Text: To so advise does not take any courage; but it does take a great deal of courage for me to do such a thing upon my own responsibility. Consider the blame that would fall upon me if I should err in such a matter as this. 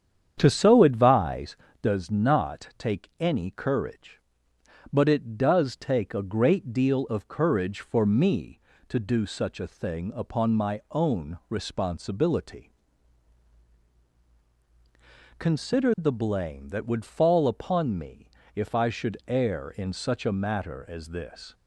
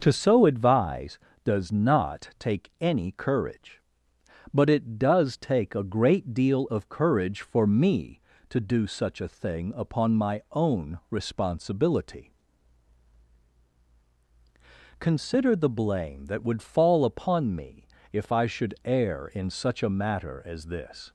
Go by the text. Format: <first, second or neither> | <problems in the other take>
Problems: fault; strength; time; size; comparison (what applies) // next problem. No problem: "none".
second | starts louder than the rest; strong; until 2.0 s; 8.5 dB // pauses between "me" and "if"; slight; at 18.2 s; 0.28 s long; slight in the second